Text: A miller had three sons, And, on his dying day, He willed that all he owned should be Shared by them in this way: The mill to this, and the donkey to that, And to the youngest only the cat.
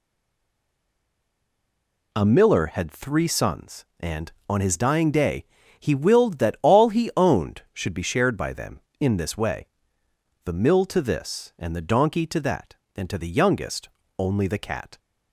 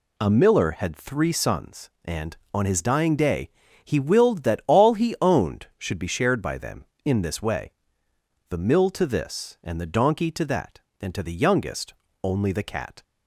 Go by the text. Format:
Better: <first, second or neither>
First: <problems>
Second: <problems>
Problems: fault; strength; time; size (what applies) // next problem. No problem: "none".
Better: second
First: stays silent before the first word; until 2.1 s; 2.1 s long // pauses between "youngest" and "only"; slight; at 13.8 s; 0.30 s long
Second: pauses between "youngest" and "only"; slight; at 11.9 s; 0.30 s long